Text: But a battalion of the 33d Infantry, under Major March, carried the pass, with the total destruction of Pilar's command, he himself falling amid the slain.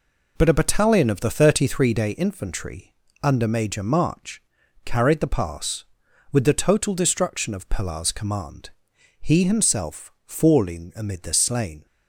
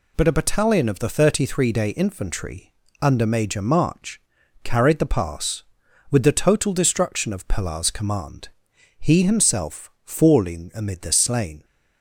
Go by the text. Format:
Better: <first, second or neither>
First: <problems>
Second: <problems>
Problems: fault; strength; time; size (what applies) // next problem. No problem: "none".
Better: second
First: starts louder than the rest; until 2.1 s; 3.5 dB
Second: none